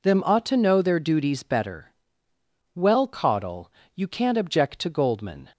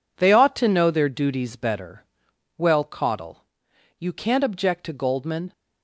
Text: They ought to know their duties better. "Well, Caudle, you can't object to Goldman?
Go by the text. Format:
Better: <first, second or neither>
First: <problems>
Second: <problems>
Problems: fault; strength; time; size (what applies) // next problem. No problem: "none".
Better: second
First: says "Them" for "They"; at 0.0 s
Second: none